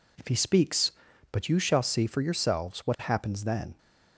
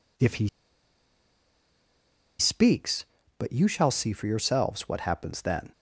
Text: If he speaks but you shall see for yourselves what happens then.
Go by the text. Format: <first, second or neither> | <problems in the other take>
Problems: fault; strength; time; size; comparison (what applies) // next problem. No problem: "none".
first | pauses between "he" and "speaks"; strong; at 0.4 s; 1.9 s long